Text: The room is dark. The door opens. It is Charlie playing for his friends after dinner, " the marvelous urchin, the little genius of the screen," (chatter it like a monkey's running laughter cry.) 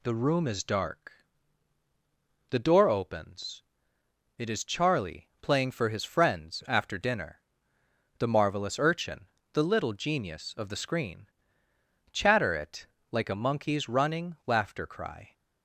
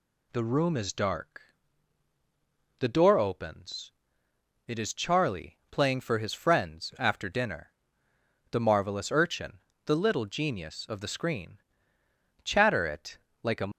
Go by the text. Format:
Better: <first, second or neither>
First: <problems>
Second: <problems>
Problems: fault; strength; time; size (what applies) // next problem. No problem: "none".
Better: first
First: pauses between "it" and "like"; slight; at 12.8 s; 0.26 s long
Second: pauses between "it" and "like"; slight; at 13.1 s; 0.26 s long // stops before "monkey's running laughter cry"; at 13.7 s